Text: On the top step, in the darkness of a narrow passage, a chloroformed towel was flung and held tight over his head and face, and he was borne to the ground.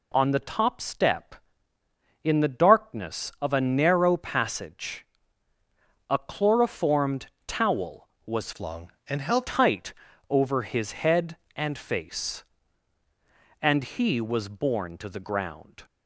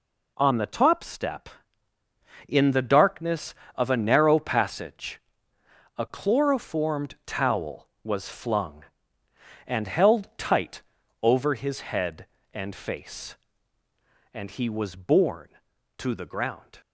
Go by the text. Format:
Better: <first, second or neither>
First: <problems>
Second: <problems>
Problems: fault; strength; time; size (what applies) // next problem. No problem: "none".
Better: second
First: pauses between "chloroformed" and "towel"; slight; at 7.2 s; 0.20 s long // changes voice from "flung" to "held"; from 8.5 to 9.4 s; 0.9 s long // pauses between "tight" and "over"; slight; at 9.9 s; 0.36 s long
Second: pauses between "tight" and "over"; at 10.8 s; 0.40 s long